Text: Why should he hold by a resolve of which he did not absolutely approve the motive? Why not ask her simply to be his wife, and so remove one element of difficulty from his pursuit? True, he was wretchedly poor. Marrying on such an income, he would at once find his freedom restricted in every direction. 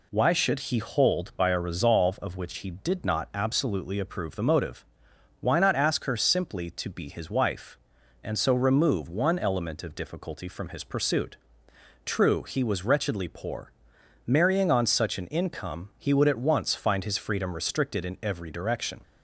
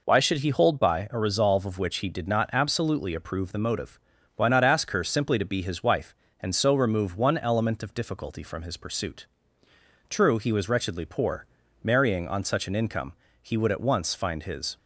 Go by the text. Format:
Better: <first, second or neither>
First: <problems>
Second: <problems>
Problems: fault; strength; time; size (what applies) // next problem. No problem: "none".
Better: first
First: none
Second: stops before "freedom restricted in every direction"; at 14.7 s